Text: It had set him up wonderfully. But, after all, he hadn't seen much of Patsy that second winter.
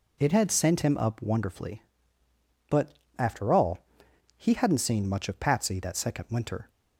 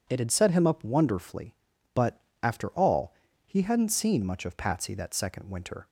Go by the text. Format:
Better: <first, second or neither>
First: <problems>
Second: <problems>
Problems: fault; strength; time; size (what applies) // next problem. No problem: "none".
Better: second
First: says "sent" for "set"; at 0.4 s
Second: none